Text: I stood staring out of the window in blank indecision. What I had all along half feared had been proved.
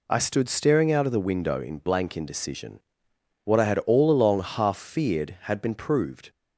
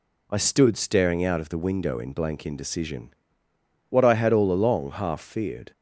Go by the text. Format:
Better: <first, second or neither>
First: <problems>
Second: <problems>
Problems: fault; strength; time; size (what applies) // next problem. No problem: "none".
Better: first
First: none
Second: stops before "had been proved"; at 5.7 s